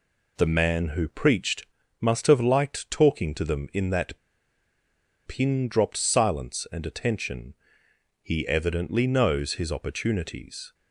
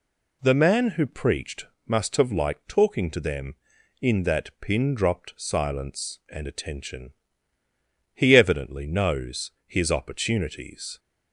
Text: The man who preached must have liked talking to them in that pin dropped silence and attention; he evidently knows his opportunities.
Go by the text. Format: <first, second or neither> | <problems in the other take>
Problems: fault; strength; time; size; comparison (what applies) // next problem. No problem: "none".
second | pauses between "preached" and "must"; slight; at 1.6 s; 0.34 s long; slight in the second // pauses between "that" and "pin"; at 4.1 s; 1.0 s long